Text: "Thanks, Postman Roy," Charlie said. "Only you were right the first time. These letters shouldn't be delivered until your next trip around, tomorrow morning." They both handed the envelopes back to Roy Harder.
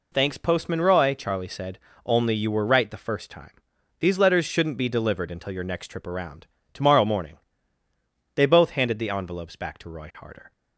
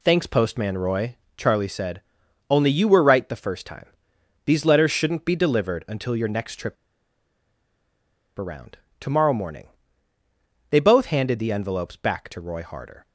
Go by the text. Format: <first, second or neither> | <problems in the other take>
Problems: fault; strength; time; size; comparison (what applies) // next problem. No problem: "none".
first | pauses between "trip" and "around"; strong; at 6.7 s; 1.6 s long